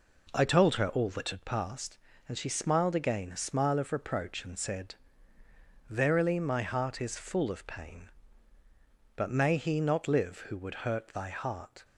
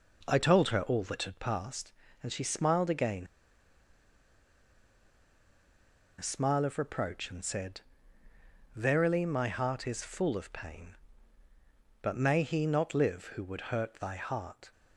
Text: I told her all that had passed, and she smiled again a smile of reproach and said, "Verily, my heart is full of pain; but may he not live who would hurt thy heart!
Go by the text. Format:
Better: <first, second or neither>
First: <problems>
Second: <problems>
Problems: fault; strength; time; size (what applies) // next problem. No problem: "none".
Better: first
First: none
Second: pauses between "again" and "a"; strong; at 3.2 s; 2.9 s long